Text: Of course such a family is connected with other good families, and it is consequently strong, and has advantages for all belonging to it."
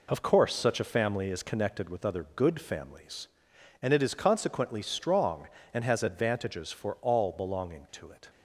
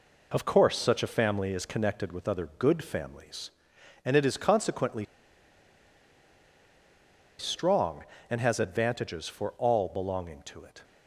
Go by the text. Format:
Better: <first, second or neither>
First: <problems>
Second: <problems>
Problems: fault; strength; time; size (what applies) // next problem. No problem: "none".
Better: first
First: none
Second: pauses between "consequently" and "strong"; strong; at 5.0 s; 2.3 s long